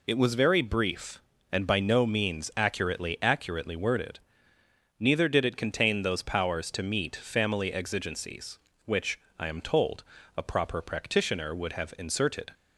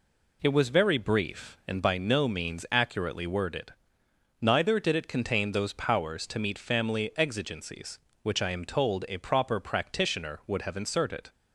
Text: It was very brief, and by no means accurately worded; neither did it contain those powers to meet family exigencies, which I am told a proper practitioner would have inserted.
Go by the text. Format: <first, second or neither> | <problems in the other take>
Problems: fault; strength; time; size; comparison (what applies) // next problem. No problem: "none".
second | says "accurately" twice; at 3.2 s // pauses between "which" and "I"; slight; at 9.2 s; 0.18 s long // pauses between "told" and "a"; slight; at 10.0 s; 0.34 s long